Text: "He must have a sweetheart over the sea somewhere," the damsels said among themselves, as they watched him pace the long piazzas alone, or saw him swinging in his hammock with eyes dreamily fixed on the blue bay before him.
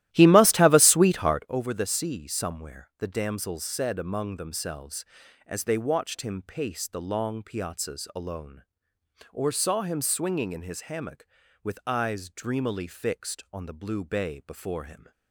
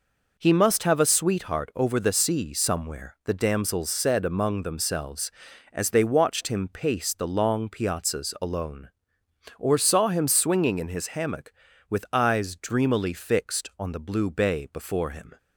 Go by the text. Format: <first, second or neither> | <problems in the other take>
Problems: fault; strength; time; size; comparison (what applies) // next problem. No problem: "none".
second | starts louder than the rest; strong; until 1.6 s; 15 dB